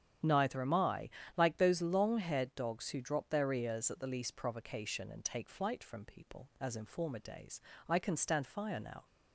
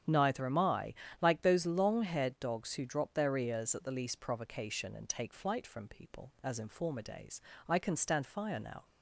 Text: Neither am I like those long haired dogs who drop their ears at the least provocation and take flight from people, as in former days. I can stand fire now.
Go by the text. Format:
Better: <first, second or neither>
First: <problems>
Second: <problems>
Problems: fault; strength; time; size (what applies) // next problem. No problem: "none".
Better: neither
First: starts louder than the rest; strong; until 1.4 s; 9 dB // pauses between "I" and "like"; slight; at 1.0 s; 0.26 s long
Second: starts louder than the rest; strong; until 1.3 s; 9 dB // pauses between "I" and "like"; slight; at 0.9 s; 0.26 s long